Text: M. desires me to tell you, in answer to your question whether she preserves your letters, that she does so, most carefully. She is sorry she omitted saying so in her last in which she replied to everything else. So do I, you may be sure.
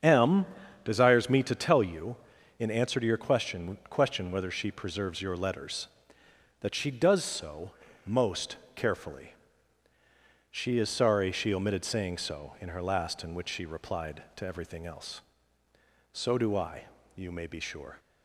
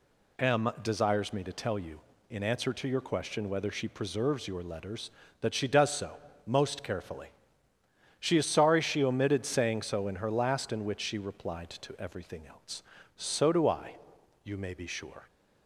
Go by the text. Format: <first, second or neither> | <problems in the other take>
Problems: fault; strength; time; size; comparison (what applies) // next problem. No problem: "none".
second | starts louder than the rest; strong; until 1.4 s; 7.5 dB // says "question" twice; at 3.8 s // pauses between "most" and "carefully"; slight; at 8.5 s; 0.18 s long